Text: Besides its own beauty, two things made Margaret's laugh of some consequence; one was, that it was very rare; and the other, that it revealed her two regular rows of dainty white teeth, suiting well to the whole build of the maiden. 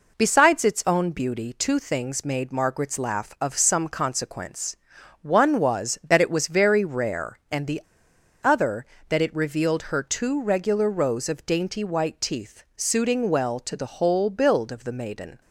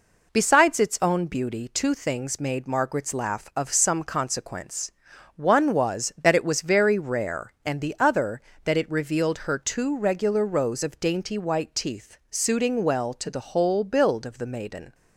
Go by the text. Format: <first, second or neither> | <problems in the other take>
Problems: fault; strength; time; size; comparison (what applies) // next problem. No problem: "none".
second | pauses between "the" and "other"; noticeable; at 7.8 s; 0.60 s long